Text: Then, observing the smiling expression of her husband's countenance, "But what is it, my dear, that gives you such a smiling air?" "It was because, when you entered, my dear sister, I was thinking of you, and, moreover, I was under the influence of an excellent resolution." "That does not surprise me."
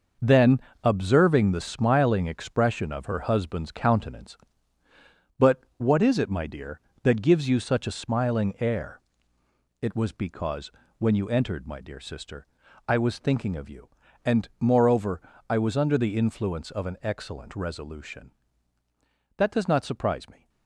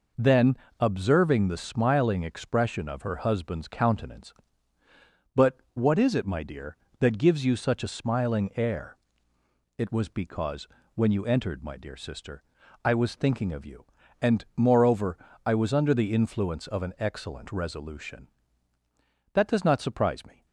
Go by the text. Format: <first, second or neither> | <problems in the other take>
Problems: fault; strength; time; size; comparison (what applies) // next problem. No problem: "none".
second | gets quieter; strong; throughout; 9 dB